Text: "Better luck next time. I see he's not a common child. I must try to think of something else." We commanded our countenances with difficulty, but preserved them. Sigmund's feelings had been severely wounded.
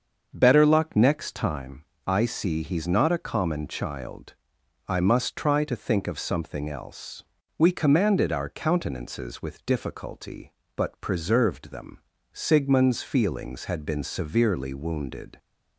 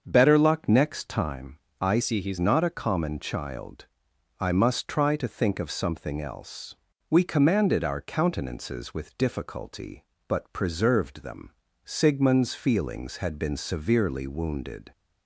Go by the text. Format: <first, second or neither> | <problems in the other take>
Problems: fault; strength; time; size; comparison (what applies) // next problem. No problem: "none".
first | starts louder than the rest; until 1.0 s; 7 dB; also in the first // changes voice from "see" to "he's"; from 2.0 to 2.3 s; 0.3 s long